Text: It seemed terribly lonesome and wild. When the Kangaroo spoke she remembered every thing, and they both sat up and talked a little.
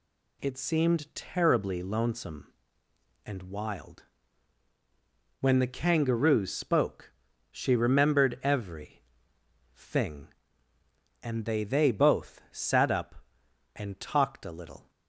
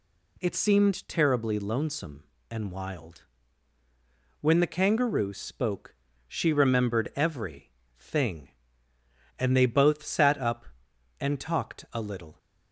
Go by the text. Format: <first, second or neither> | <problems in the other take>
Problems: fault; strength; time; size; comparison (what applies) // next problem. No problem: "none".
second | pauses between "spoke" and "she"; at 7.1 s; 0.40 s long; slight in the second // pauses between "every" and "thing"; noticeable; at 9.0 s; 0.74 s long; slight in the second // says "they" twice; at 11.6 s